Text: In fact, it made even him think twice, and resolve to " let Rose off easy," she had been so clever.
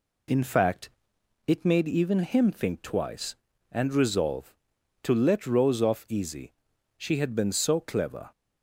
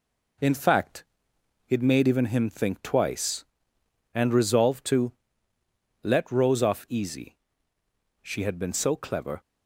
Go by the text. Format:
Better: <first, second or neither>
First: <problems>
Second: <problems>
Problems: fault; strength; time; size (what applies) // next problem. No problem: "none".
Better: first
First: none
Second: gets quieter; throughout; 6 dB